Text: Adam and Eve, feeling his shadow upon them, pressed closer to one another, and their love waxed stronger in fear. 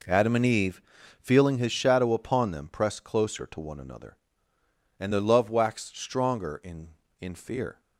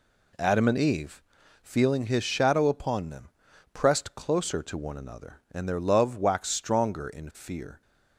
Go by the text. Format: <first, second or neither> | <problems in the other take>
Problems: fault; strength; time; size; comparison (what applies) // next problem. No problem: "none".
second | says "in" twice; at 7.1 s